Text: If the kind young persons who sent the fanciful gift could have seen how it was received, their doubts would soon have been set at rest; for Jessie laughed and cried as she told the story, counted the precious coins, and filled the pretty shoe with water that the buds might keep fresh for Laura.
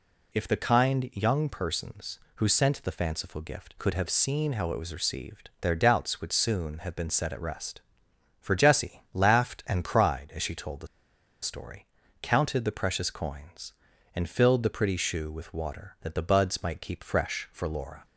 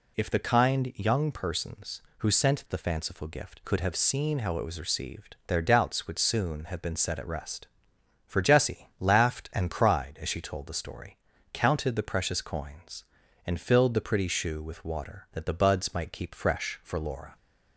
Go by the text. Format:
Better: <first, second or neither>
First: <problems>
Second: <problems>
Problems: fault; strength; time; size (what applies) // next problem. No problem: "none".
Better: second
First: pauses between "the" and "story"; noticeable; at 10.8 s; 0.55 s long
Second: none